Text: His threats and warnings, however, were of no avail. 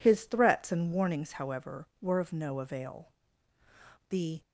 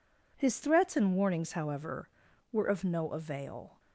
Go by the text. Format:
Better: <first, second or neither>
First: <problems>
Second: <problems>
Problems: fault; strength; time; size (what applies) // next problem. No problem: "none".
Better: second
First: goes on to say "The"; slight; from 4.0 s on; 0.32 s long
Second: none